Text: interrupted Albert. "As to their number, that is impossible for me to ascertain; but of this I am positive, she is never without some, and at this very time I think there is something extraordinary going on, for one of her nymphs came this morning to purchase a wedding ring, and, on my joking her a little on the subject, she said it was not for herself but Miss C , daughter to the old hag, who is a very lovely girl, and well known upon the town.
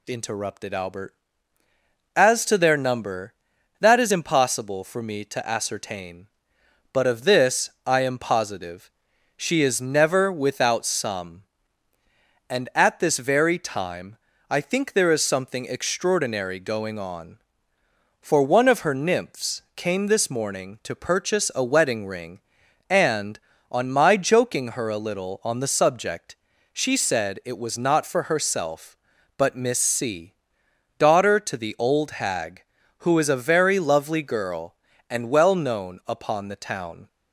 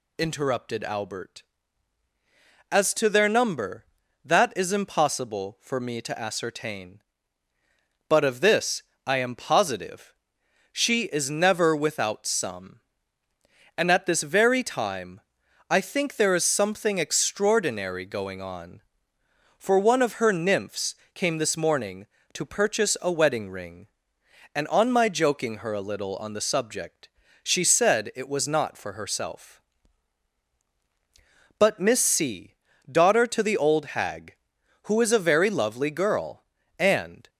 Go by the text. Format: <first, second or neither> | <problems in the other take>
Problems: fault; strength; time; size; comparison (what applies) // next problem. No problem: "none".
first | pauses between "this" and "I"; slight; at 8.8 s; 0.24 s long; slight in the first // pauses between "time" and "I"; noticeable; at 15.2 s; 0.48 s long; slight in the first // pauses between "nymphs" and "came"; slight; at 20.9 s; 0.20 s long // stops before "well known upon the town"; at 37.2 s